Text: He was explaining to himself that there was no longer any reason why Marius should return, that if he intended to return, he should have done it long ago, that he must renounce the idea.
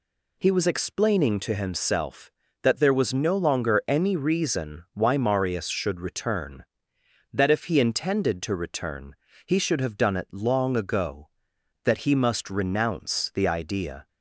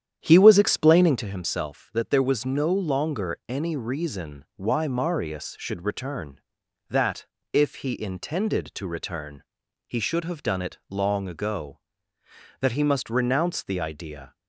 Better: first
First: none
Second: starts louder than the rest; strong; until 1.3 s; 9.5 dB // pauses between "that" and "if"; slight; at 7.2 s; 0.28 s long

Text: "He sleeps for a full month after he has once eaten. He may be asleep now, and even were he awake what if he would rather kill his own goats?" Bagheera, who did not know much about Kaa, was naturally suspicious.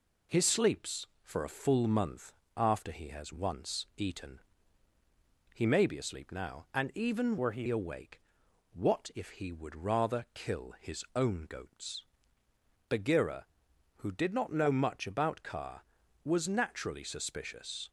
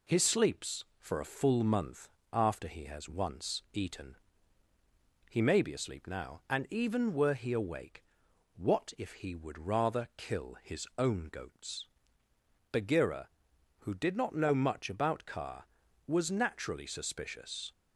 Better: second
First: pauses between "month" and "after"; slight; at 2.3 s; 0.24 s long // changes voice from "were" to "he"; from 7.3 to 7.6 s; 0.3 s long // pauses between "awake" and "what"; noticeable; at 8.2 s; 0.52 s long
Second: pauses between "month" and "after"; slight; at 2.0 s; 0.24 s long // pauses between "awake" and "what"; noticeable; at 8.0 s; 0.52 s long

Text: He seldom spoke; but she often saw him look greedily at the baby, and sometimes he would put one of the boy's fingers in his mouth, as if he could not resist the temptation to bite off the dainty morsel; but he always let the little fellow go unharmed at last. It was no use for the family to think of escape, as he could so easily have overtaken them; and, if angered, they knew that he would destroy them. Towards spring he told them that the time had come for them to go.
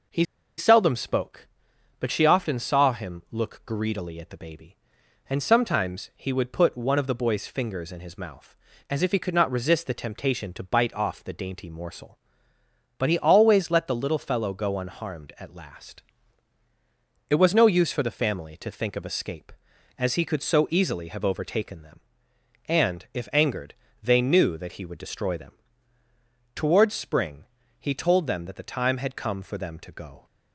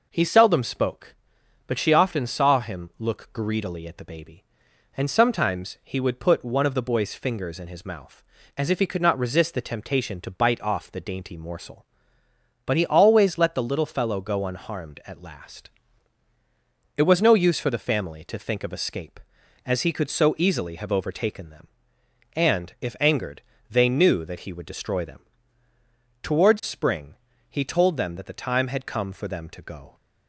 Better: second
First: pauses between "He" and "seldom"; slight; at 0.2 s; 0.32 s long // pauses between "spring" and "he"; slight; at 27.4 s; 0.36 s long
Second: pauses between "spring" and "he"; slight; at 27.1 s; 0.36 s long

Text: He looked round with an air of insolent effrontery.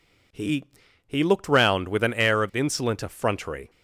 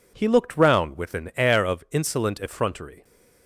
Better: second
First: says "He" twice; at 1.0 s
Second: none

